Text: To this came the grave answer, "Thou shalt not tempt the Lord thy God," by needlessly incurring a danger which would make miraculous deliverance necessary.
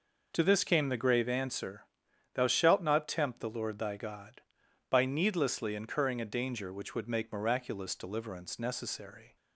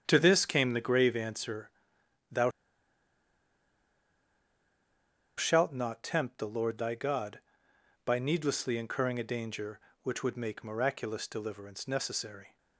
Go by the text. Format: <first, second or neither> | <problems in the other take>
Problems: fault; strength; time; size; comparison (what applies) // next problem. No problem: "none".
first | starts louder than the rest; strong; until 1.0 s; 8.5 dB // pauses between "Thou" and "shalt"; strong; at 2.5 s; 2.8 s long